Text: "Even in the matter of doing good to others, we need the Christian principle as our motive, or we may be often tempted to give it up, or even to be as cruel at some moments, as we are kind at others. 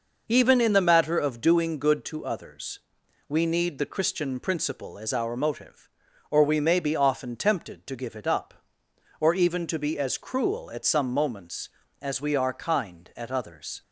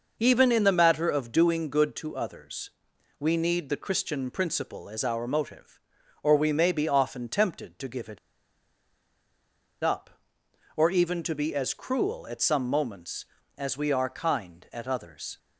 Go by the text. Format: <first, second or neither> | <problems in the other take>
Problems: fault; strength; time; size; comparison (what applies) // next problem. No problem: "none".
first | pauses between "it" and "up"; strong; at 8.1 s; 1.6 s long